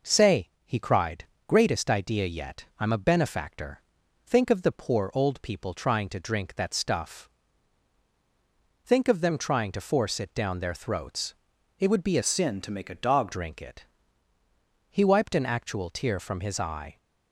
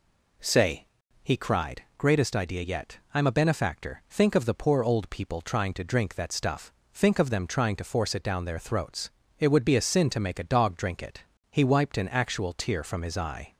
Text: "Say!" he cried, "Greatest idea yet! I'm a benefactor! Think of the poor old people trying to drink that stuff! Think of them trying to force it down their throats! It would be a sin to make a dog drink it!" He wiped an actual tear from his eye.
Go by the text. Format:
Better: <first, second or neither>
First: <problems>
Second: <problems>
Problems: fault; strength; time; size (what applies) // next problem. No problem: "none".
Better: second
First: changes voice from "sin" to "dog"; from 12.2 to 13.3 s; 1.1 s long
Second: none